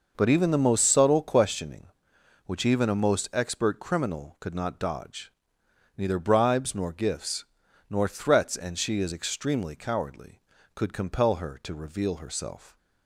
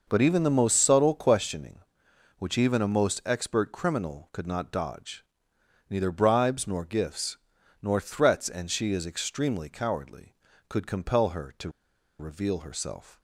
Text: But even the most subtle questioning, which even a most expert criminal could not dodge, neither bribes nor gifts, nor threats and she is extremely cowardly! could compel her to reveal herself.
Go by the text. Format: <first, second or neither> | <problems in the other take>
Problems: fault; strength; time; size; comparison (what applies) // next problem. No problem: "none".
first | pauses between "to" and "reveal"; noticeable; at 11.7 s; 0.49 s long